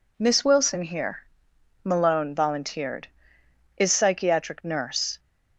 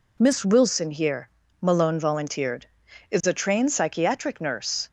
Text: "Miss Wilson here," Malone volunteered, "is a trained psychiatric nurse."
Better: second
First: skips "a trained"; at 3.9 s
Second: none

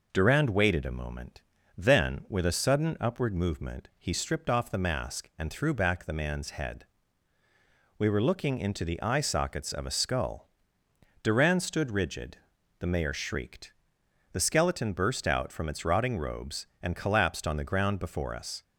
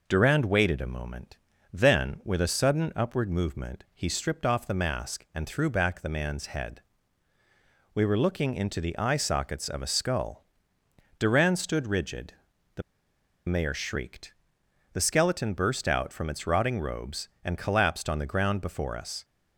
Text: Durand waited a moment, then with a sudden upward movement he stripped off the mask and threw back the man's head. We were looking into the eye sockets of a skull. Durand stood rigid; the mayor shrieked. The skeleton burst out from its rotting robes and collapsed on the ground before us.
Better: first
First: none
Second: pauses between "the" and "mayor"; noticeable; at 12.8 s; 0.66 s long

